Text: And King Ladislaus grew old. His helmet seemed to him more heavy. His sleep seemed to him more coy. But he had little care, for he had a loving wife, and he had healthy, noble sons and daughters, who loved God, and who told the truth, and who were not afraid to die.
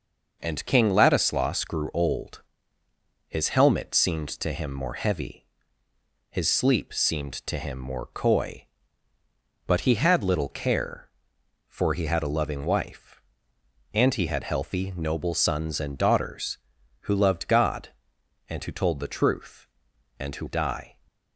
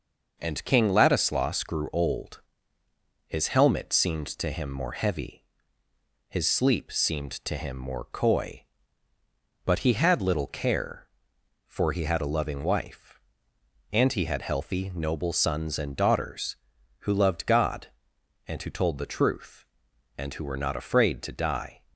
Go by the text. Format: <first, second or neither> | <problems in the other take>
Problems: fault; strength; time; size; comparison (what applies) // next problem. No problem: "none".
second | skips "were not afraid to"; at 20.4 s